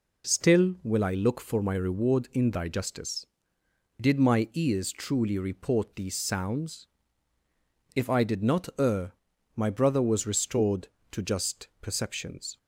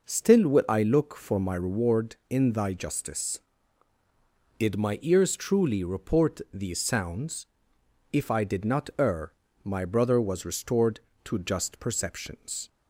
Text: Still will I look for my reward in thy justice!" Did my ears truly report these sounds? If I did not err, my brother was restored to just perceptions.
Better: neither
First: none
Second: none

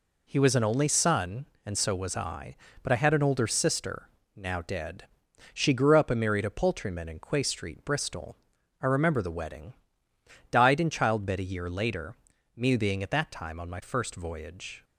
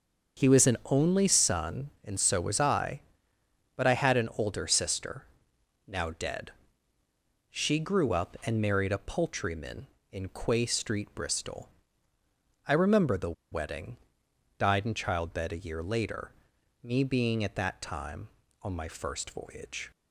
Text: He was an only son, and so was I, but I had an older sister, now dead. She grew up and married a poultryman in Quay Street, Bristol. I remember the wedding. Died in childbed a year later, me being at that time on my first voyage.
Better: first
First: none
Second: starts louder than the rest; until 1.4 s; 6.5 dB // pauses between "the" and "wedding"; slight; at 13.3 s; 0.19 s long

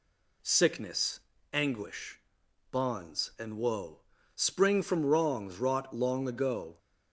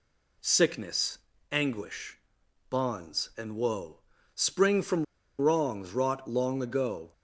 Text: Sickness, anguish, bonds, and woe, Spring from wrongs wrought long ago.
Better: first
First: none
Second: pauses between "from" and "wrongs"; slight; at 5.0 s; 0.34 s long

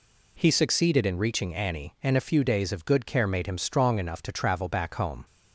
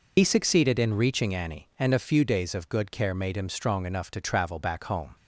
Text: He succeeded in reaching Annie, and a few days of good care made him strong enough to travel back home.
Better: first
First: none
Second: loses the start of "He"; at 0.1 s; 70 ms

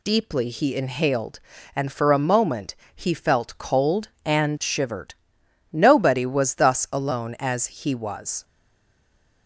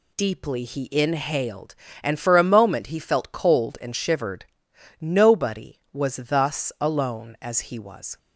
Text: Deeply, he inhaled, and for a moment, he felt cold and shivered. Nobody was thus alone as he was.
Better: second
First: stays silent after the last word; from 8.4 s on; 1.0 s long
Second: none

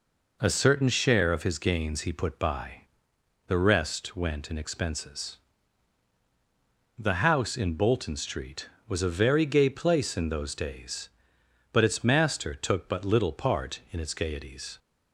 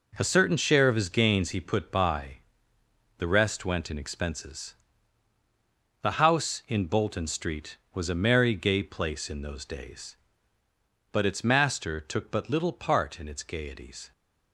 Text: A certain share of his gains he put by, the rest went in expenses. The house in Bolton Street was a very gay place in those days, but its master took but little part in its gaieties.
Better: first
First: none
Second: says "merry" for "very"; at 8.1 s

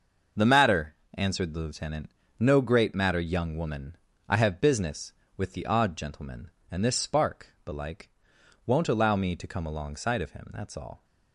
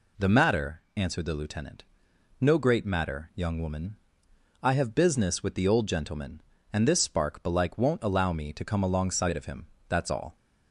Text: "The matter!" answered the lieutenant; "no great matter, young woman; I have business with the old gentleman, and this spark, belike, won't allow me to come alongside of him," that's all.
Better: second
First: starts louder than the rest; noticeable; until 1.5 s; 6 dB // says "odd" for "old"; at 5.6 s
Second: none

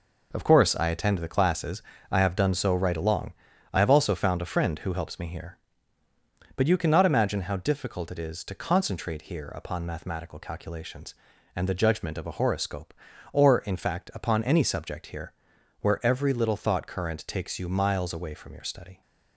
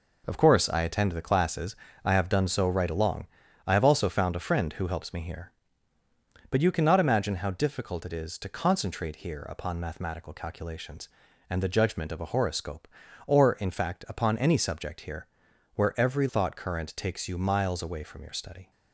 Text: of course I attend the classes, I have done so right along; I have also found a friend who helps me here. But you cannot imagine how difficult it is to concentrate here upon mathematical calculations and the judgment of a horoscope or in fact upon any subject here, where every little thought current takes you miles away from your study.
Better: first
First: none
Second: skips "little"; at 16.2 s

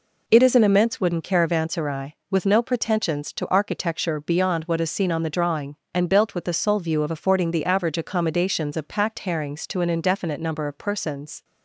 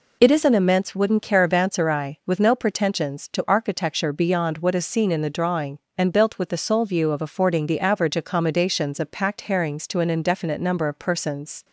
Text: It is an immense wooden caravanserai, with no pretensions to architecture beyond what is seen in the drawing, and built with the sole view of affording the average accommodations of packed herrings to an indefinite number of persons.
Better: second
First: says "on" for "in"; at 5.1 s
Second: none

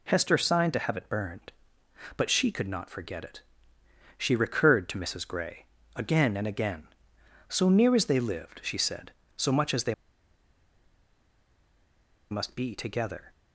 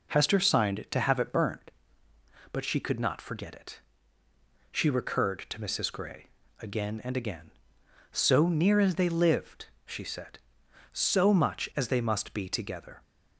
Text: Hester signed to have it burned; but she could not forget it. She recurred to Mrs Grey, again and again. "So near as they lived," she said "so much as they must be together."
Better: second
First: pauses between "they" and "must"; strong; at 9.9 s; 2.3 s long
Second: none

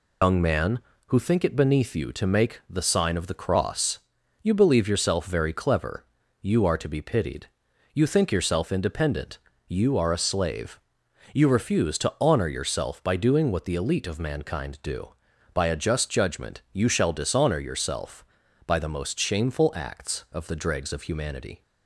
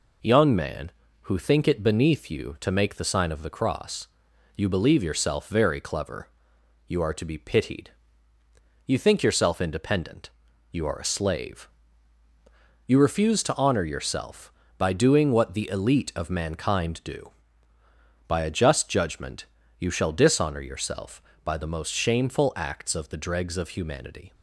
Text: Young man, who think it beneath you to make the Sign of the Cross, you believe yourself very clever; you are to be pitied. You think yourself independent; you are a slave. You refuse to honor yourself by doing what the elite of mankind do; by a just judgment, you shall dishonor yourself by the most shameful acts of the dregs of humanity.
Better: second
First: loses the start of "Young"; at 0.2 s; 140 ms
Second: none

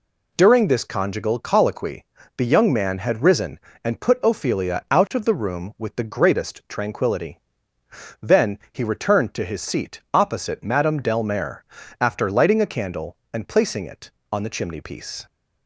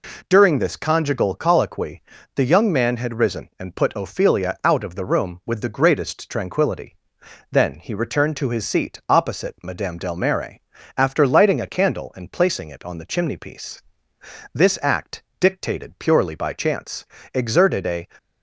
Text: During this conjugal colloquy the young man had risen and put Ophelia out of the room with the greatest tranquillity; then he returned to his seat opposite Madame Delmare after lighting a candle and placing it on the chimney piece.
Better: first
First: pauses between "colloquy" and "the"; slight; at 2.0 s; 0.32 s long // pauses between "Delmare" and "after"; at 11.6 s; 0.40 s long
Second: pauses between "colloquy" and "the"; slight; at 2.0 s; 0.32 s long // pauses between "Delmare" and "after"; at 10.5 s; 0.38 s long // goes on to say "This act dictated purely by chance exerted a"; strong; from 14.5 s on; 3.5 s long

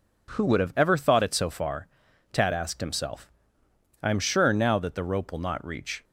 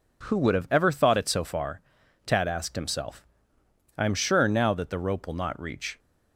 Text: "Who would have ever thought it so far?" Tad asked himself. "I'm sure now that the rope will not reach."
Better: neither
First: none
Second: none

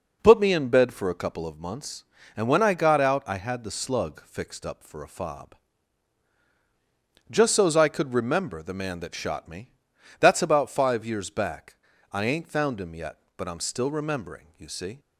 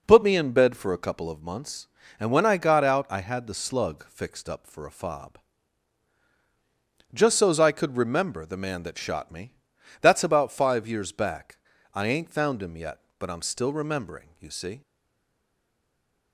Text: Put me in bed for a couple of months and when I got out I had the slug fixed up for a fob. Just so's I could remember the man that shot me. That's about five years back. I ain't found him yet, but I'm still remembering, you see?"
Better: first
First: none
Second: stays silent after the last word; noticeable; from 14.8 s on; 1.5 s long

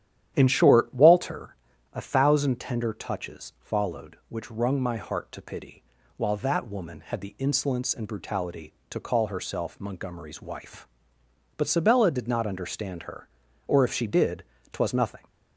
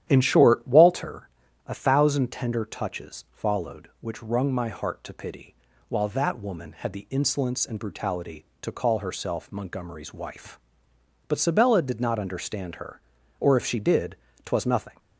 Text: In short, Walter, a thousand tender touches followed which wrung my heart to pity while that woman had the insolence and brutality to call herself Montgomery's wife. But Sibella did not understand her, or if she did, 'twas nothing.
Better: neither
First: starts louder than the rest; strong; until 1.3 s; 11 dB // pauses between "pity" and "while"; slight; at 5.8 s; 0.32 s long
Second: starts louder than the rest; strong; until 1.0 s; 11 dB // pauses between "pity" and "while"; slight; at 5.5 s; 0.32 s long

